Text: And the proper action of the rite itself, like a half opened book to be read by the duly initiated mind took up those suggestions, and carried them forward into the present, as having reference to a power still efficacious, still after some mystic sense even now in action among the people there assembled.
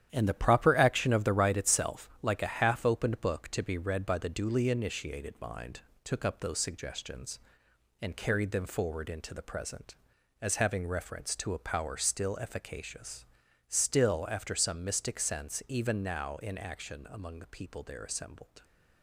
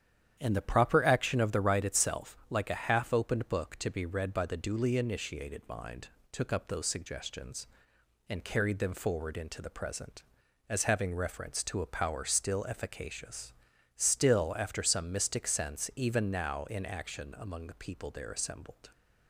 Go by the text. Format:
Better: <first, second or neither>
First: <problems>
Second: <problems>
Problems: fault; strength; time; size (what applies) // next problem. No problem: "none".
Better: second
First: gets quieter; strong; throughout; 8.5 dB // starts louder than the rest; strong; until 1.1 s; 10.5 dB // pauses between "mind" and "took"; slight; at 5.8 s; 0.22 s long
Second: starts louder than the rest; strong; until 1.4 s; 9.5 dB // pauses between "mind" and "took"; slight; at 6.0 s; 0.22 s long